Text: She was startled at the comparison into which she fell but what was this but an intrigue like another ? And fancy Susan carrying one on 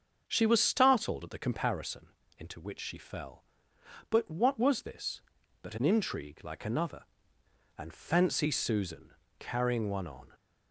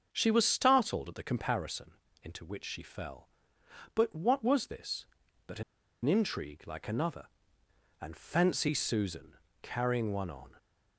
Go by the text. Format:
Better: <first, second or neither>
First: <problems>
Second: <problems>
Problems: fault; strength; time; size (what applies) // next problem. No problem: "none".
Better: first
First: starts louder than the rest; until 1.2 s; 7 dB // pauses between "comparison" and "into"; slight; at 2.0 s; 0.30 s long // pauses between "Susan" and "carrying"; slight; at 9.1 s; 0.26 s long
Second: starts louder than the rest; until 1.1 s; 7 dB // pauses between "comparison" and "into"; slight; at 1.9 s; 0.30 s long // pauses between "an" and "intrigue"; at 5.6 s; 0.42 s long // pauses between "Susan" and "carrying"; slight; at 9.3 s; 0.26 s long